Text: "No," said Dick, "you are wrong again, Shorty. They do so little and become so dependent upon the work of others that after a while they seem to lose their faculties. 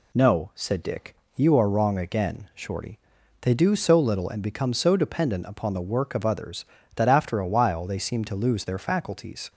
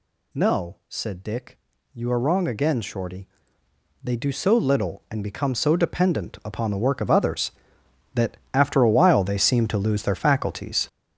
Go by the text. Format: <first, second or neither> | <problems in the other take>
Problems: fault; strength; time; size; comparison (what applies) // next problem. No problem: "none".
first | gets louder; strong; throughout; 8.5 dB // pauses between "that" and "after"; slight; at 8.3 s; 0.16 s long